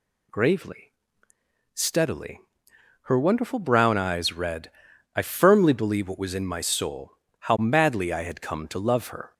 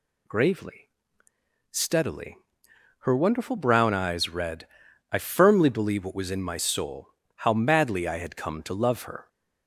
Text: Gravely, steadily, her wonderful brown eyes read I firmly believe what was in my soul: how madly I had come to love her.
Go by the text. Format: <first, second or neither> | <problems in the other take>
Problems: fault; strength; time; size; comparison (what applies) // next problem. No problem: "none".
neither | pauses between "read" and "I"; noticeable; the same in both